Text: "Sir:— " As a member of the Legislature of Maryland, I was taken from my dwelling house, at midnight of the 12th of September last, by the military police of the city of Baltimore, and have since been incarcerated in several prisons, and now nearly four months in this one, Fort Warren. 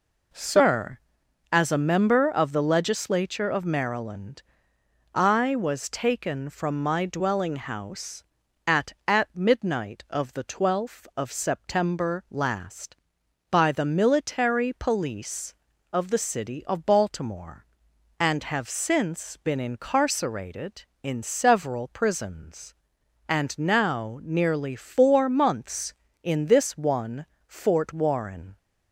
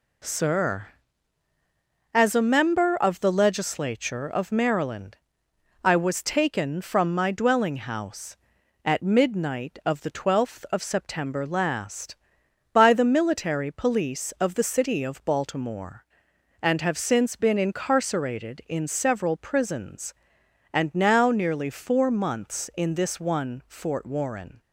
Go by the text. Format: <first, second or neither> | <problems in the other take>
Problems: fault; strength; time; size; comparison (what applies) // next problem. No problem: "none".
second | says "at" twice; at 9.0 s